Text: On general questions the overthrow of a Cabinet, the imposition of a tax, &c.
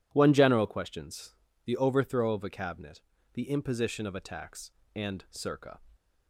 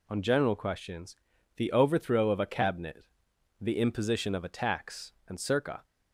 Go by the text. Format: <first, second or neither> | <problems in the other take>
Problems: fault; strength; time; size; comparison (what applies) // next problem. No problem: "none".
second | says "One" for "On"; at 0.1 s // pauses between "questions" and "the"; slight; at 1.3 s; 0.30 s long; also in the second